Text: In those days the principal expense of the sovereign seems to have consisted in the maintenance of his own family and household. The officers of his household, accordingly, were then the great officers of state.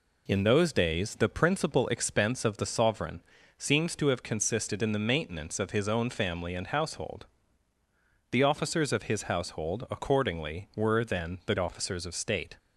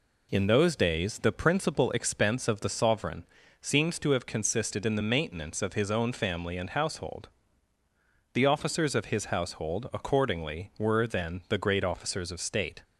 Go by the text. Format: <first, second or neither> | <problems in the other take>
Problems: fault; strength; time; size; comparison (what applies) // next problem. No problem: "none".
second | pauses between "sovereign" and "seems"; slight; at 3.2 s; 0.34 s long; slight in the second // skips "great"; at 11.5 s